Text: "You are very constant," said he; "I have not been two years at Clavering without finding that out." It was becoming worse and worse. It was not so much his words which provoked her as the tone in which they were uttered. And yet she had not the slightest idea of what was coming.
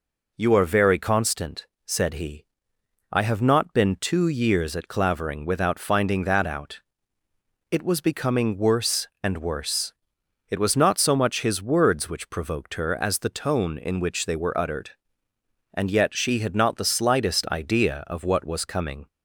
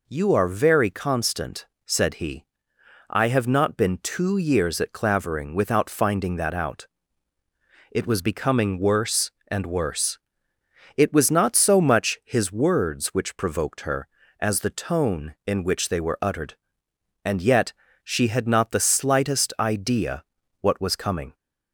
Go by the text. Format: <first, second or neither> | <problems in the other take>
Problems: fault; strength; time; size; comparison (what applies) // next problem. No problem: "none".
first | pauses between "yet" and "she"; slight; at 17.7 s; 0.32 s long // skips "of"; at 20.4 s